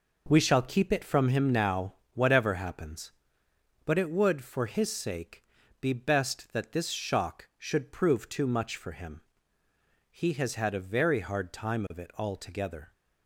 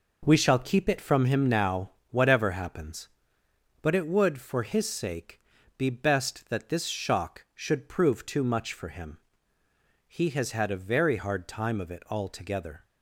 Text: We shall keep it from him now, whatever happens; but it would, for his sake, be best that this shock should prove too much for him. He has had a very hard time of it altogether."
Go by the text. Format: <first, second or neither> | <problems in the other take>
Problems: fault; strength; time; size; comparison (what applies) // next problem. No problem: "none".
neither | none